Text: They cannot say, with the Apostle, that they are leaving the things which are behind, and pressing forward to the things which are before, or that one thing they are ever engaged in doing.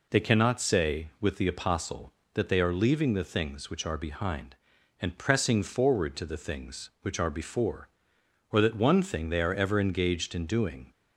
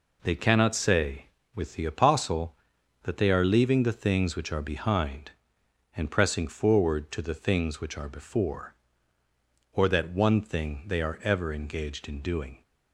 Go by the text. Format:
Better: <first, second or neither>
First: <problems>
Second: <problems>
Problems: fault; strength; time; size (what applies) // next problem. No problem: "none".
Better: neither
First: none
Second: none